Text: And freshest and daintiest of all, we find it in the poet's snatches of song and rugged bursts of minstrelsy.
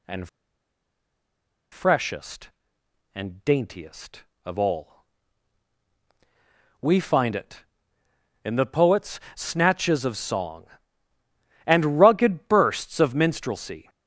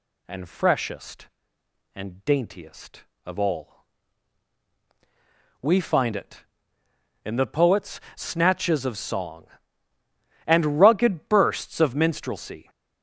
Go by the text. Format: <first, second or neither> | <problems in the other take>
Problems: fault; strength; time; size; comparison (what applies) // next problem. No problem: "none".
second | pauses between "And" and "freshest"; strong; at 0.2 s; 1.4 s long